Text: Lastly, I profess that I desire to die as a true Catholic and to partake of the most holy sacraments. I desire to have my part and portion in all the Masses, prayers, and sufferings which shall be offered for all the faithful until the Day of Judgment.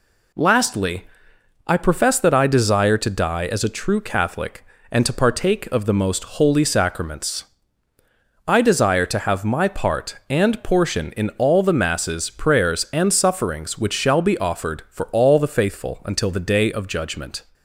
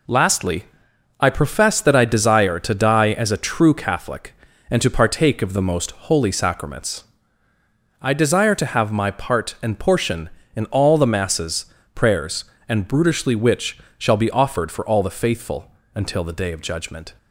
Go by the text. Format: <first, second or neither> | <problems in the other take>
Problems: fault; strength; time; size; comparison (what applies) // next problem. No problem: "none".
first | says "brutishly" for "sufferings"; at 12.8 s // pauses between "which" and "shall"; slight; at 13.7 s; 0.18 s long // pauses between "faithful" and "until"; slight; at 15.7 s; 0.24 s long